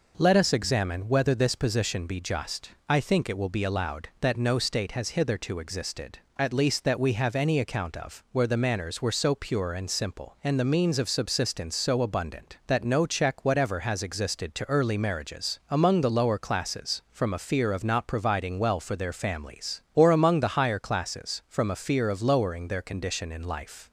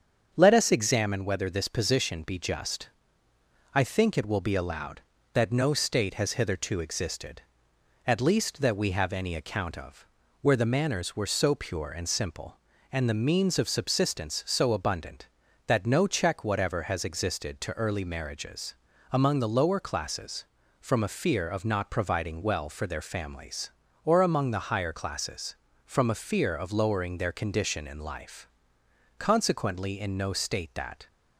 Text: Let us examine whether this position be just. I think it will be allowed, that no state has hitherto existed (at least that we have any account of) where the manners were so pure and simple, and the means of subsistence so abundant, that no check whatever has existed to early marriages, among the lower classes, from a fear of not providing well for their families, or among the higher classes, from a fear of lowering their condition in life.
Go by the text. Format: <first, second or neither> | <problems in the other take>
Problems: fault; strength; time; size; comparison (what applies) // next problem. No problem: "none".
first | starts louder than the rest; strong; until 1.3 s; 7 dB // goes on to say "Consequently in no state that"; strong; from 29.1 s on; 1.8 s long